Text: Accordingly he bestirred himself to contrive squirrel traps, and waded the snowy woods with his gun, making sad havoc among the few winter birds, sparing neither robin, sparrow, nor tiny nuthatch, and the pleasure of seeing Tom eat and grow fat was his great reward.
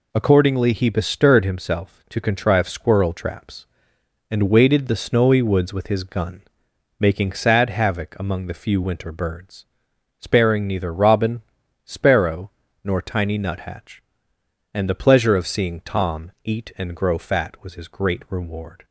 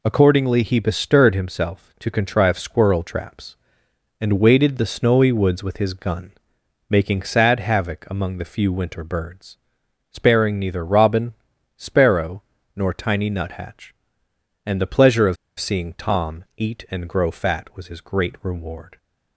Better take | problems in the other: first | pauses between "of" and "seeing"; slight; at 15.3 s; 0.23 s long

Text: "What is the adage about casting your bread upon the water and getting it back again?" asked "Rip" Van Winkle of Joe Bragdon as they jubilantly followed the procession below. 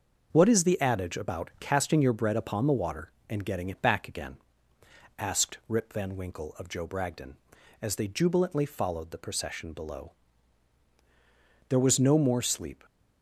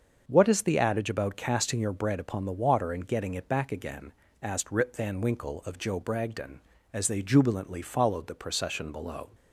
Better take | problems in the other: second | starts louder than the rest; until 1.3 s; 6.5 dB; also in the second // goes on to say "There was no more sleep"; noticeable; from 11.6 s on; 1.1 s long

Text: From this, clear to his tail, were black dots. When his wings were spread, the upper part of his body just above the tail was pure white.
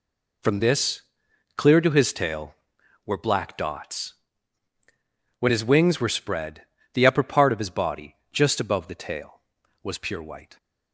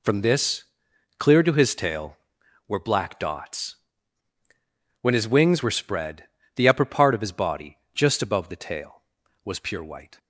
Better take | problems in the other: neither | pauses between "body" and "just"; slight; the same in both

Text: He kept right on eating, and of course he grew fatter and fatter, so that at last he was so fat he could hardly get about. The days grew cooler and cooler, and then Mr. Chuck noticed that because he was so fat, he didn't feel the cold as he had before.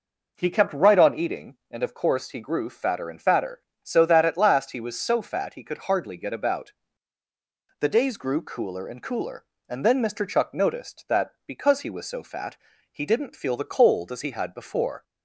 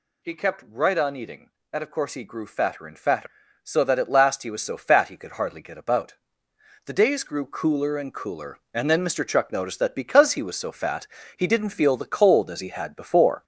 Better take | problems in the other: first | gets louder; noticeable; throughout; 5.5 dB

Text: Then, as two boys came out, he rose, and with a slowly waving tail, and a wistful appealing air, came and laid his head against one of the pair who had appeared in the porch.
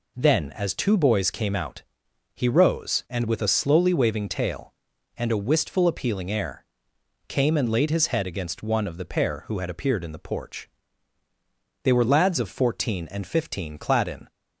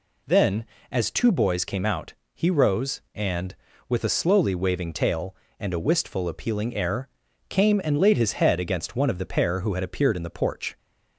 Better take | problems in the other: second | goes on to say "They were lads of fourteen and fifteen clad in"; strong; from 11.8 s on; 2.4 s long

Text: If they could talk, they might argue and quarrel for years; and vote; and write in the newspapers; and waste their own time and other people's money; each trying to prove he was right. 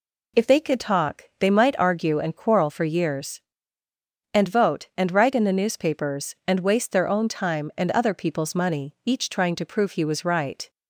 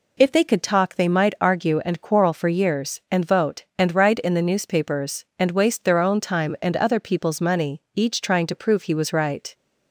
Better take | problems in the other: neither | none

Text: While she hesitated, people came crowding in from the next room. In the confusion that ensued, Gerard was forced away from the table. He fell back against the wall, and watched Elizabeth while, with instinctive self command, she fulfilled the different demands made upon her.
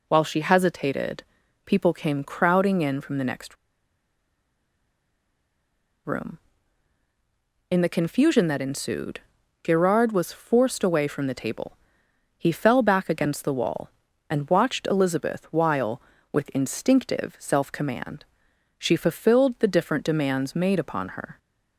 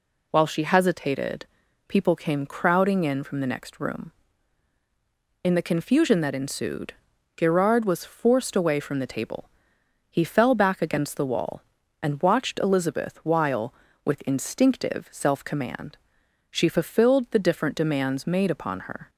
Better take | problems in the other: second | pauses between "next" and "room"; strong; at 3.5 s; 2.5 s long

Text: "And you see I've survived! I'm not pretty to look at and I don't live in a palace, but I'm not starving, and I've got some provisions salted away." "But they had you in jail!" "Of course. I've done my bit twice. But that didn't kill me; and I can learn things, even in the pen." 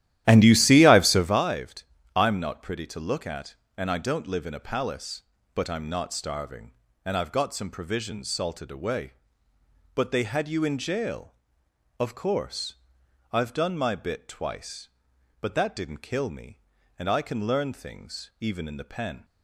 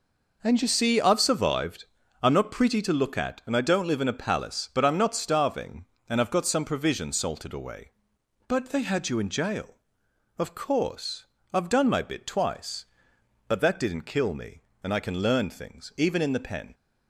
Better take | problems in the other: second | starts louder than the rest; strong; until 1.4 s; 13 dB

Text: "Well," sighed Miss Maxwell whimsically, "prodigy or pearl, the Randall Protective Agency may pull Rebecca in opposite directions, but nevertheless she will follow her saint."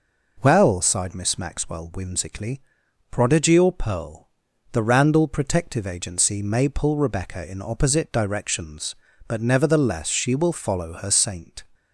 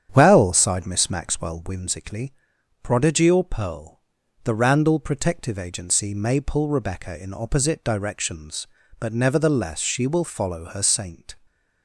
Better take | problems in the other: first | starts louder than the rest; strong; until 1.9 s; 9 dB

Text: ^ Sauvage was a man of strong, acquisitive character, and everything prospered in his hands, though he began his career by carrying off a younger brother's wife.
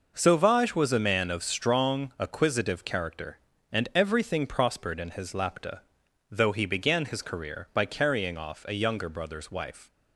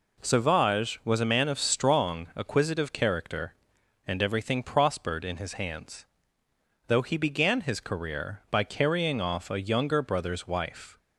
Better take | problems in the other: second | says "lapta" for "hands"; at 5.3 s

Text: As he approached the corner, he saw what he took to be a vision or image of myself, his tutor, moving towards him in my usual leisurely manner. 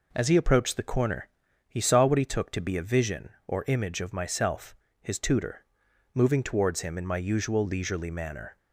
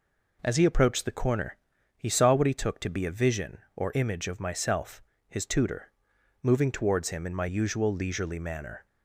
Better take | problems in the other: neither | none

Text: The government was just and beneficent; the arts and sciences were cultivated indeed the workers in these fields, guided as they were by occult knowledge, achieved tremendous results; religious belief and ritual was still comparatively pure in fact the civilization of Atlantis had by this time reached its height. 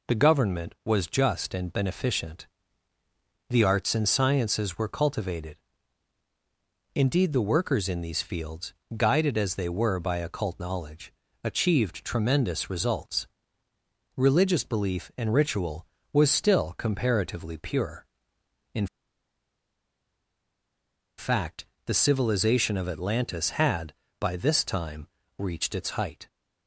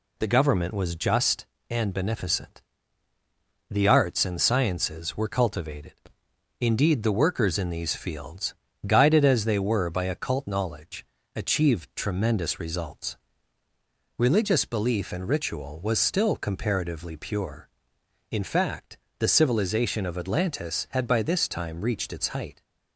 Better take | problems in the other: second | pauses between "cultivated" and "indeed"; strong; at 5.5 s; 1.3 s long; noticeable in the second // pauses between "in" and "fact"; strong; at 18.8 s; 2.3 s long // pauses between "fact" and "the"; slight; at 21.6 s; 0.22 s long; slight in the second // pauses between "time" and "reached"; slight; at 25.0 s; 0.30 s long

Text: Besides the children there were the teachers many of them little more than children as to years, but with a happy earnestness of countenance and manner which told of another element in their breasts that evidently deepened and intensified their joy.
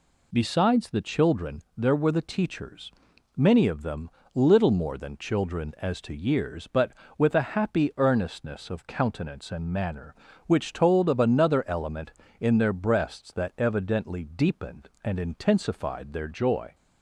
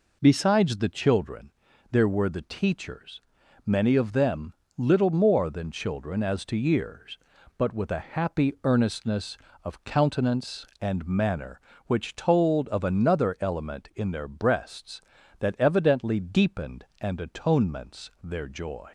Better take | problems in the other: first | pauses between "children" and "there"; at 1.5 s; 0.42 s long // pauses between "teachers" and "many"; at 3.2 s; 0.44 s long; also in the first // pauses between "them" and "little"; slight; at 4.5 s; 0.24 s long; slight in the first // says "atonements" for "intensified"; at 17.2 s

